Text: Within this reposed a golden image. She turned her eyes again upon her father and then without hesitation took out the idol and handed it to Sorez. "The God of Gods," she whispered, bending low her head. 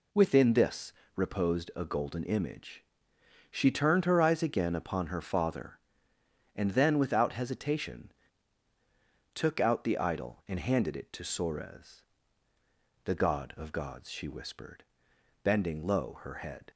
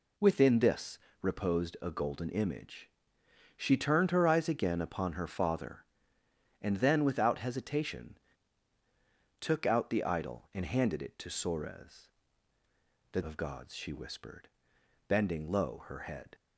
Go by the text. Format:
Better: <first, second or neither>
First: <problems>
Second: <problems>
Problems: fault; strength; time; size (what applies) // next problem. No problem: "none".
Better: first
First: pauses between "this" and "reposed"; slight; at 0.9 s; 0.24 s long // pauses between "hesitation" and "took"; at 8.1 s; 1.2 s long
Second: pauses between "this" and "reposed"; slight; at 0.9 s; 0.24 s long // pauses between "hesitation" and "took"; at 8.1 s; 1.2 s long // skips "God"; at 13.2 s